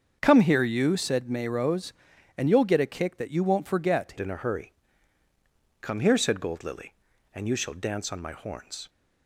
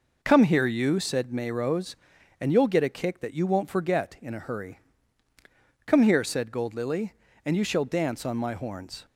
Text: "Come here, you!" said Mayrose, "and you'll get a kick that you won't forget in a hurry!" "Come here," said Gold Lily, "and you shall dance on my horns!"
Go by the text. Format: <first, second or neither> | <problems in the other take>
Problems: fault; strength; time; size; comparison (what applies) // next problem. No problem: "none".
second | starts louder than the rest; until 1.2 s; 7 dB // changes voice at "in"; from 4.1 s on; 4.7 s long